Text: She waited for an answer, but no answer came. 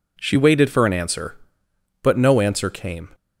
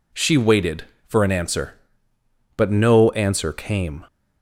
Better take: neither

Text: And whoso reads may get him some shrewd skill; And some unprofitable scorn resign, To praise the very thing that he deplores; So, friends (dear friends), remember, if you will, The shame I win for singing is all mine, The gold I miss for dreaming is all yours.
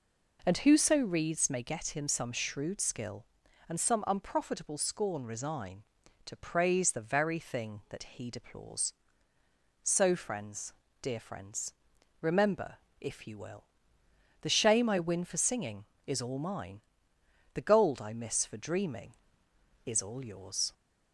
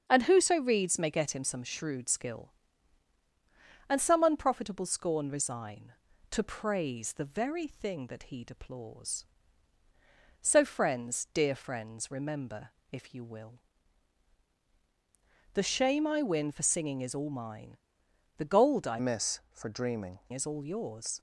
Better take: first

